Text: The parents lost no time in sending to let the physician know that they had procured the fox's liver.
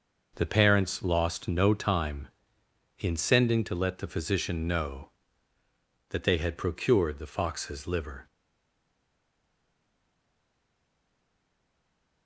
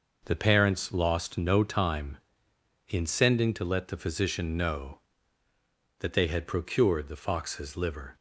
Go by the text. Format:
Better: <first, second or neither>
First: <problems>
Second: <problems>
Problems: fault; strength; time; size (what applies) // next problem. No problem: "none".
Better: second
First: stays silent after the last word; strong; from 8.2 s on; 4.0 s long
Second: none